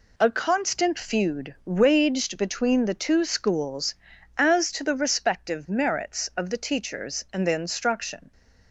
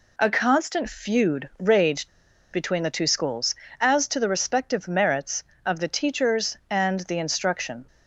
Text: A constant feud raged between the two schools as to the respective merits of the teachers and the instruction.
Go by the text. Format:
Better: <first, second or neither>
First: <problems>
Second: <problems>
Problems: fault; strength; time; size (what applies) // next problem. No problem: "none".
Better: first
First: none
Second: pauses between "raged" and "between"; at 2.0 s; 0.45 s long